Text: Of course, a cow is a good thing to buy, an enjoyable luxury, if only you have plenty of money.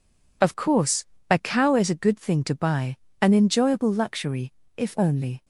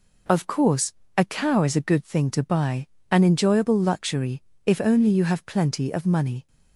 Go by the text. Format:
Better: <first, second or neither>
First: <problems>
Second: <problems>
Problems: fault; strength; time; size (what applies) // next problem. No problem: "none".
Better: second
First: stops before "you have plenty of money"; at 5.4 s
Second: none